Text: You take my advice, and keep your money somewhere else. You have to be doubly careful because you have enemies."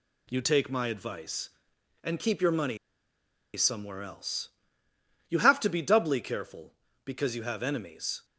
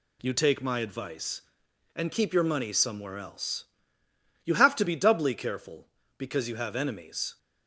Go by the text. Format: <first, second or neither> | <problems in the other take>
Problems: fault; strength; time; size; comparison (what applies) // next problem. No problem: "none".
second | pauses between "money" and "somewhere"; noticeable; at 2.7 s; 0.79 s long